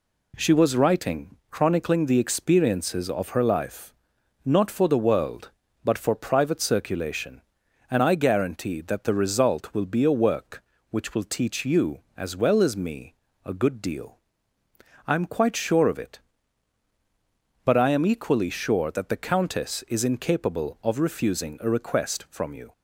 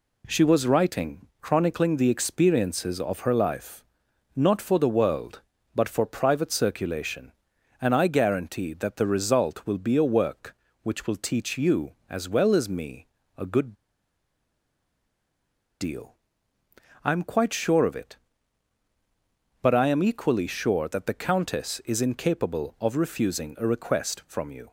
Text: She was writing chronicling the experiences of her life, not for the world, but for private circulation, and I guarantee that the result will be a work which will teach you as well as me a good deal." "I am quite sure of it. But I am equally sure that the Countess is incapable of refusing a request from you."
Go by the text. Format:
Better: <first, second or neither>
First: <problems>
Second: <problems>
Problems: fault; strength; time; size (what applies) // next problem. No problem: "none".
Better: first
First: pauses between "me" and "a"; slight; at 13.1 s; 0.32 s long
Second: pauses between "me" and "a"; slight; at 13.0 s; 0.32 s long // pauses between "good" and "deal"; strong; at 13.7 s; 2.0 s long